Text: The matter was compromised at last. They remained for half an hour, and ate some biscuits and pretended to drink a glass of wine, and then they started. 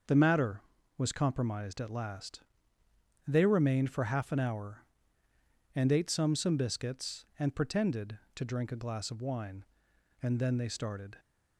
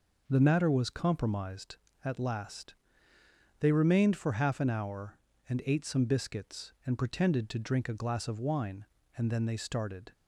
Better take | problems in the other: second | starts louder than the rest; until 1.4 s; 6 dB // says "some" twice; at 6.3 s

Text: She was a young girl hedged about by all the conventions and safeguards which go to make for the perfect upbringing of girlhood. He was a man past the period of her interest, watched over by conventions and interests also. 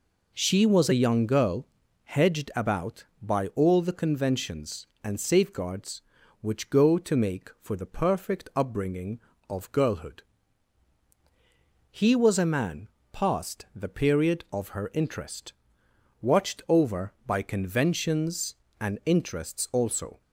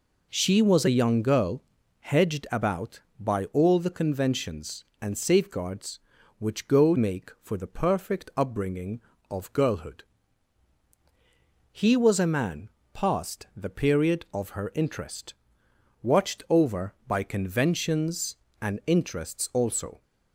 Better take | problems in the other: first | pauses between "girl" and "hedged"; at 1.6 s; 0.38 s long; also in the first // skips "to"; at 6.9 s // pauses between "man" and "past"; slight; at 12.6 s; 0.24 s long; slight in the first

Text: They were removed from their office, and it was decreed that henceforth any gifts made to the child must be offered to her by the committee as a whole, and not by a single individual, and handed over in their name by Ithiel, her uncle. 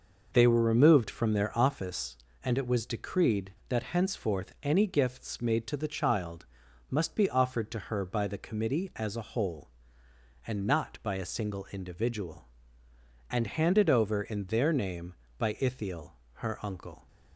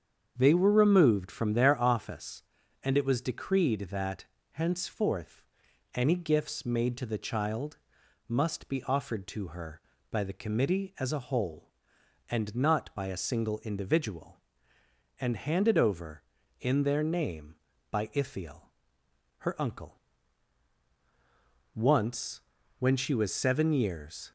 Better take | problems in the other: first | starts louder than the rest; strong; until 1.3 s; 7.5 dB // pauses between "that" and "henceforth"; slight; at 4.2 s; 0.28 s long // pauses between "henceforth" and "any"; noticeable; at 5.4 s; 0.52 s long // pauses between "child" and "must"; noticeable; at 7.7 s; 0.50 s long; also in the first // goes on to say "Once when she was seven years"; strong; from 21.7 s on; 2.5 s long

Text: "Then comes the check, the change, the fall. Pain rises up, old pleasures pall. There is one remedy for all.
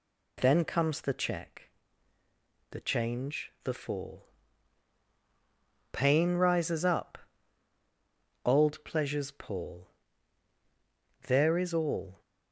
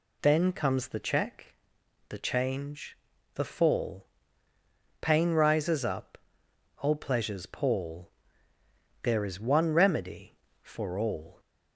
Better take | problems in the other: second | skips "one remedy for"; at 11.7 s

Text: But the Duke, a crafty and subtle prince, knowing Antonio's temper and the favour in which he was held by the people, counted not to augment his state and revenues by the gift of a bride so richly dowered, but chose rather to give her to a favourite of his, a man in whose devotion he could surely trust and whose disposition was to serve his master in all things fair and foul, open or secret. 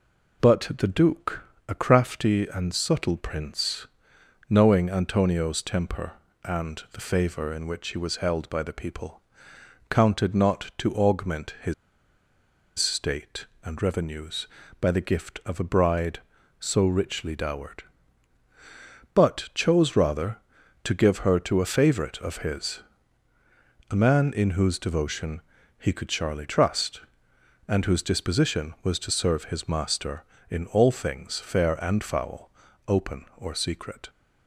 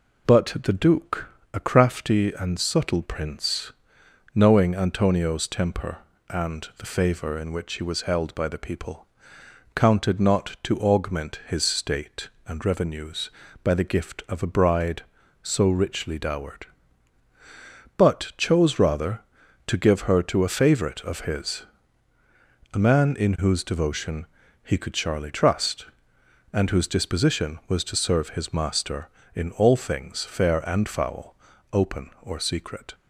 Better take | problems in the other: second | pauses between "his" and "state"; at 11.7 s; 1.0 s long // pauses between "devotion" and "he"; slight; at 25.4 s; 0.36 s long; slight in the second

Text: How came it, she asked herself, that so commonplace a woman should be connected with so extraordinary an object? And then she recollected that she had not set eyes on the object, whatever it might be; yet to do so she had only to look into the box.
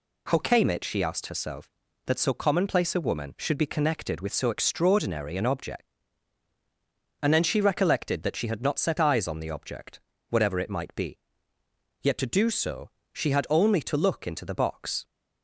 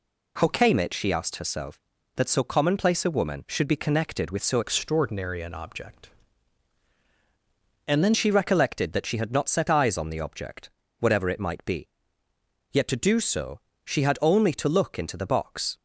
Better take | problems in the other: first | changes voice from "extraordinary" to "then"; from 4.6 to 8.1 s; 3.5 s long // pauses between "so" and "she"; slight; at 13.6 s; 0.24 s long; slight in the first

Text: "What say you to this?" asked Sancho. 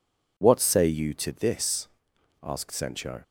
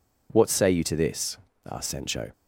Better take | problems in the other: neither | none

